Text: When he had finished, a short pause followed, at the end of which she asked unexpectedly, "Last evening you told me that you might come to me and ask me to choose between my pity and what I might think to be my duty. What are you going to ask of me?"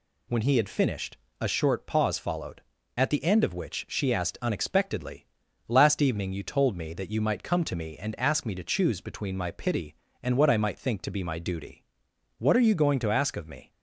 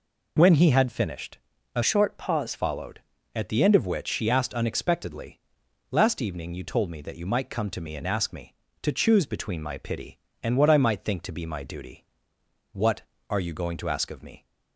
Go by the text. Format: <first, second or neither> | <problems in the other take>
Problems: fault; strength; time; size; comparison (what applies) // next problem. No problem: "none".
first | changes voice from "short" to "pause"; from 1.8 to 2.5 s; 0.7 s long